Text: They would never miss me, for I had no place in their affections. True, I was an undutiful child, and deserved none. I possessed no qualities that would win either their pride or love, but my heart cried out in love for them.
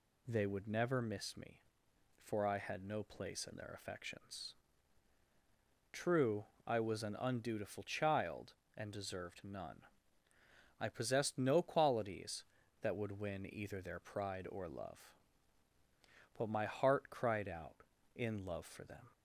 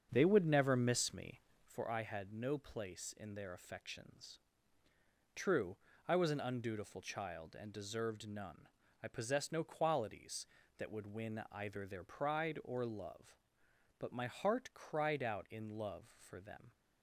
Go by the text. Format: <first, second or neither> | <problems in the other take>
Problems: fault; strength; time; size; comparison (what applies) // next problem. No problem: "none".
first | starts louder than the rest; strong; until 1.9 s; 7 dB